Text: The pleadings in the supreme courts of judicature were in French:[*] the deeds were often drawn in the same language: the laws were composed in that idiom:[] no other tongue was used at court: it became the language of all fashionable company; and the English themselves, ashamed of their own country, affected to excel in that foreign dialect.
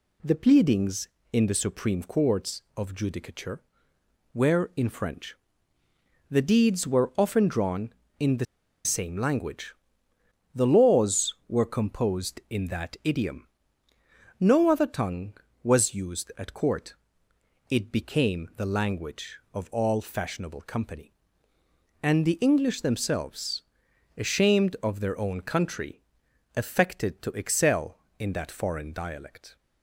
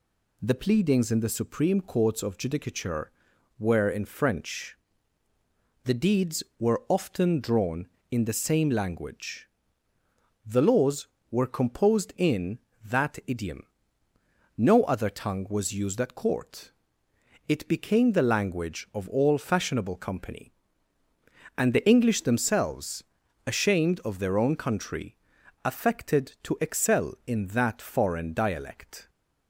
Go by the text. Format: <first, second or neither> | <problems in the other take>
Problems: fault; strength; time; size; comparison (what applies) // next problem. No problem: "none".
second | pauses between "the" and "same"; at 8.4 s; 0.40 s long